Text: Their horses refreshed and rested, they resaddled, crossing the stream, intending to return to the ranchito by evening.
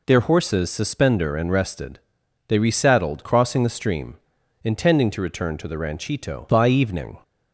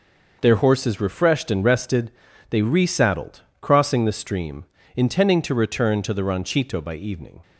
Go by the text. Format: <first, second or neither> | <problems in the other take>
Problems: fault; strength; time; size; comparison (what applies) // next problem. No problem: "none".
second | says "suspender" for "refreshed"; at 0.7 s